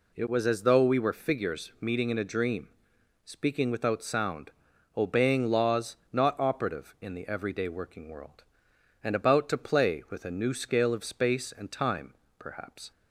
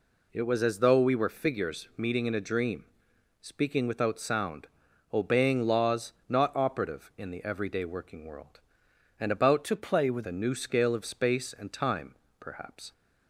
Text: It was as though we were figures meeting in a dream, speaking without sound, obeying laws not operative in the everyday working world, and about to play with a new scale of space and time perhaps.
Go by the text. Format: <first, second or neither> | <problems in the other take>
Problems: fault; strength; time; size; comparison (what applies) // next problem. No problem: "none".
first | pauses between "laws" and "not"; slight; at 6.1 s; 0.16 s long; slight in the first // changes voice from "to" to "with"; from 9.6 to 10.2 s; 0.6 s long // pauses between "time" and "perhaps"; slight; at 12.1 s; 0.26 s long; slight in the first